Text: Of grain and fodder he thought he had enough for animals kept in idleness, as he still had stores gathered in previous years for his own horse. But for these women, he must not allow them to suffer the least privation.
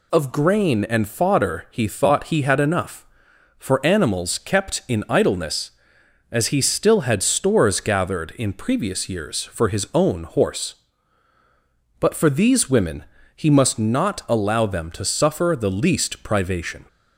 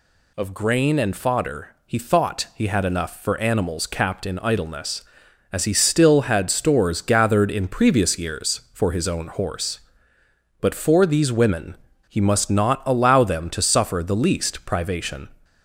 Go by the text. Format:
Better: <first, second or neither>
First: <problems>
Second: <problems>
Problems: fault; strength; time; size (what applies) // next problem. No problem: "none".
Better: first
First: none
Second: pauses between "fodder" and "he"; slight; at 1.6 s; 0.16 s long // says "capped" for "kept"; at 3.8 s